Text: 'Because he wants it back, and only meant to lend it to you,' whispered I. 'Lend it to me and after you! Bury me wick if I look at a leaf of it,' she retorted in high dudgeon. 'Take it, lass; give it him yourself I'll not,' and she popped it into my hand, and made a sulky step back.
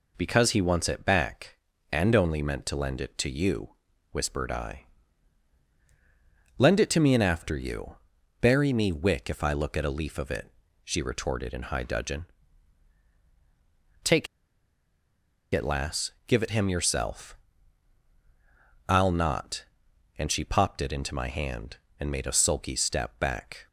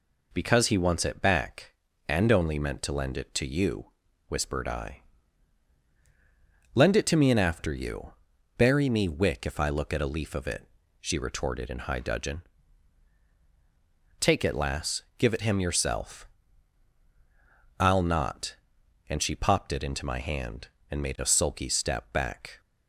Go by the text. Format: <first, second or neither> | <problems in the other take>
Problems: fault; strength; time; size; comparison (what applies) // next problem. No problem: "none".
second | pauses between "Take" and "it"; strong; at 14.2 s; 1.2 s long // pauses between "yourself" and "I'll"; strong; at 17.3 s; 1.5 s long; strong in the second